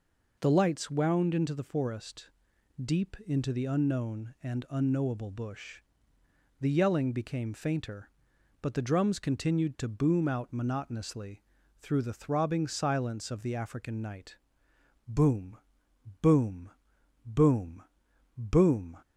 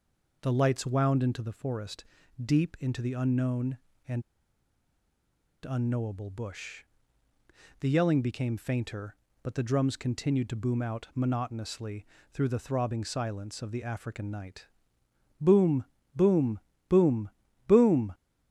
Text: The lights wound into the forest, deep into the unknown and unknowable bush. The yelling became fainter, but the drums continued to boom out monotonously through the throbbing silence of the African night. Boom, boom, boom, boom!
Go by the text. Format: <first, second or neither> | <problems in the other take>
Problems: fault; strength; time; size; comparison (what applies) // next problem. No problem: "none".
first | pauses between "and" and "unknowable"; strong; at 4.2 s; 1.4 s long // pauses between "monotonously" and "through"; slight; at 12.0 s; 0.28 s long; slight in the first